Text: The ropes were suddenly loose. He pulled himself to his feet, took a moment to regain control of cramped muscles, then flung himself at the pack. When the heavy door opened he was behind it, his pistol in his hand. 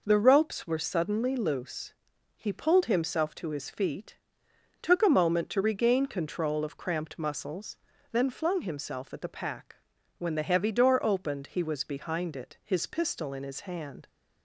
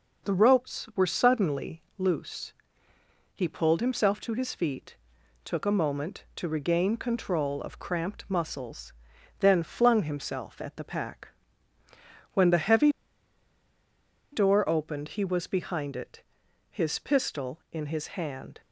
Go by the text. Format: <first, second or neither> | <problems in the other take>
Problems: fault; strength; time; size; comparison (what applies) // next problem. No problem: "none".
first | pauses between "suddenly" and "loose"; slight; at 1.8 s; 0.16 s long // pauses between "heavy" and "door"; strong; at 12.9 s; 1.4 s long